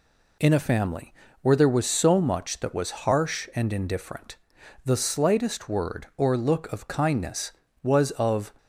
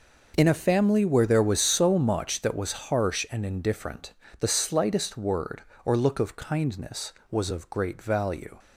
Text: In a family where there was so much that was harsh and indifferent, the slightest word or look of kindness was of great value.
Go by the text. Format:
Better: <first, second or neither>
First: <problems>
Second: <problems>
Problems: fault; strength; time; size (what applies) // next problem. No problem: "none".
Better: second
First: pauses between "family" and "where"; slight; at 1.1 s; 0.28 s long // stops before "great value"; at 8.5 s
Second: none